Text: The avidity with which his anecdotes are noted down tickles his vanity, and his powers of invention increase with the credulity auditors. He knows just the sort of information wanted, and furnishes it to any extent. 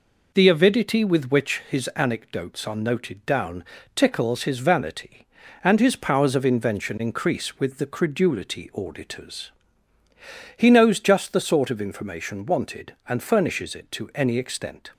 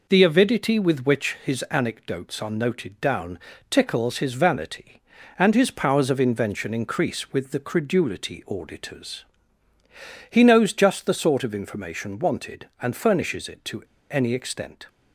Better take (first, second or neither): first